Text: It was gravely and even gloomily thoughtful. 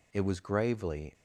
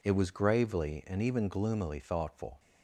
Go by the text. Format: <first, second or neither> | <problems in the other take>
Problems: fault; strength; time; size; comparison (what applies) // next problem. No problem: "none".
second | stops before "and even gloomily thoughtful"; at 1.1 s